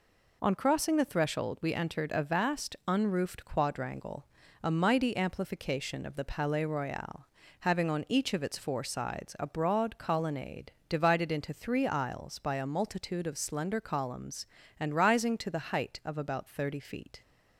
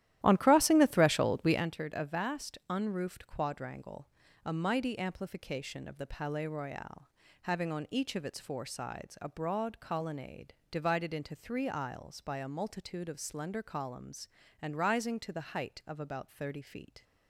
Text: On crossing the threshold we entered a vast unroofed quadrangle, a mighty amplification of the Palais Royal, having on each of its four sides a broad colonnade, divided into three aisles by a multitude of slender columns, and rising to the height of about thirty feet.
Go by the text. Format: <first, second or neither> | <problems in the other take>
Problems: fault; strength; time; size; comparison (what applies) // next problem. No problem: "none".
first | starts louder than the rest; strong; until 1.7 s; 13 dB